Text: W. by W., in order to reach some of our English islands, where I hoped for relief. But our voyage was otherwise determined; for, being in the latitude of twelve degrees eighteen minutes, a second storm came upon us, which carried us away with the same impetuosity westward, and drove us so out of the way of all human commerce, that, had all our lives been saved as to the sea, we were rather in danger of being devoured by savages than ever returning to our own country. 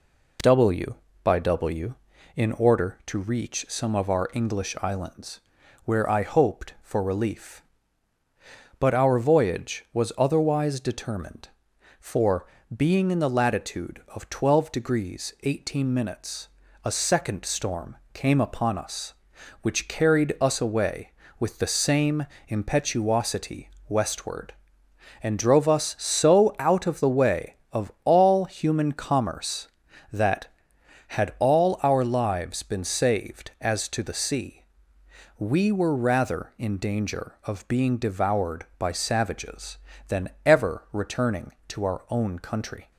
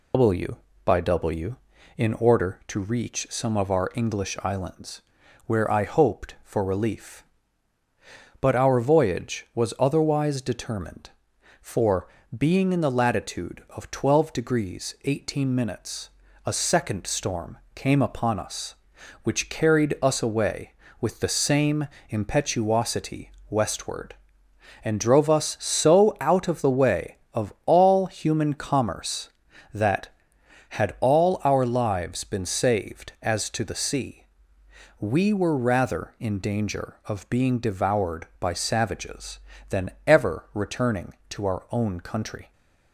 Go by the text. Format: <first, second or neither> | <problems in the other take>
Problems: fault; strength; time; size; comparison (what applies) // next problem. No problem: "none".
first | loses the start of "W"; at 0.1 s; 135 ms // pauses between "storm" and "came"; slight; at 17.5 s; 0.18 s long; slight in the first // pauses between "same" and "impetuosity"; slight; at 21.8 s; 0.24 s long; slight in the first // pauses between "impetuosity" and "westward"; slight; at 23.3 s; 0.20 s long; slight in the first // pauses between "than" and "ever"; slight; at 39.9 s; 0.16 s long; slight in the first